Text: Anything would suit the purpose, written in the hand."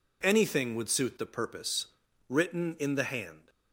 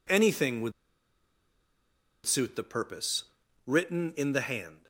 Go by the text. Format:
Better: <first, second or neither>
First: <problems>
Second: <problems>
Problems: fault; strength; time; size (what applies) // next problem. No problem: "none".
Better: first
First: none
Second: pauses between "would" and "suit"; strong; at 0.7 s; 1.5 s long